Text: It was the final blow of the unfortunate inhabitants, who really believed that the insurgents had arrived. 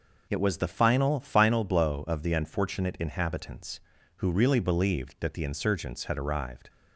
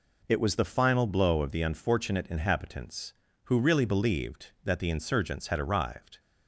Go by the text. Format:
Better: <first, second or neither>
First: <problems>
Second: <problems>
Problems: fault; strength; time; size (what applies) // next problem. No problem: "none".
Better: second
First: says "final" twice; at 1.2 s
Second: none